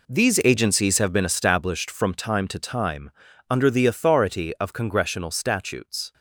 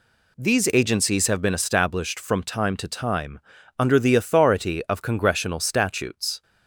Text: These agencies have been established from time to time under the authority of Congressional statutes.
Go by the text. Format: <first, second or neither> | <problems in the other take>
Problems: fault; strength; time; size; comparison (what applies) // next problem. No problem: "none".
second | gets quieter; strong; throughout; 11.5 dB // pauses between "time" and "under"; at 3.0 s; 0.40 s long; also in the second